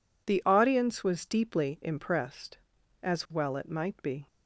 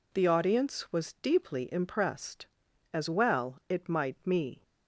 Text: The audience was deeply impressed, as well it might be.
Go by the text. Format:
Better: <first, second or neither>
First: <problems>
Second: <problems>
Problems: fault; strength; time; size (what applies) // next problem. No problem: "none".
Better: first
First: none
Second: says "me" for "be"; at 4.2 s